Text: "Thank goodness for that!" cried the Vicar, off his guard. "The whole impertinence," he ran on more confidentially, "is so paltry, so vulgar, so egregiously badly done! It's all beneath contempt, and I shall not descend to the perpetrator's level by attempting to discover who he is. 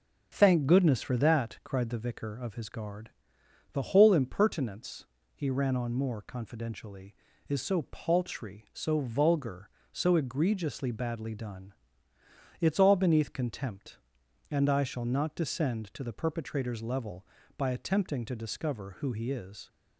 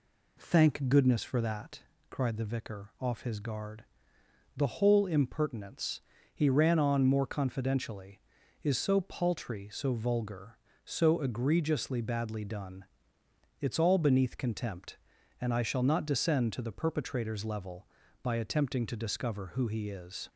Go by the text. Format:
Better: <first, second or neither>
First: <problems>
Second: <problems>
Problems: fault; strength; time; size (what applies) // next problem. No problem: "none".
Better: second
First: starts louder than the rest; until 1.3 s; 7 dB // says "of" for "off"; at 2.3 s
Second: none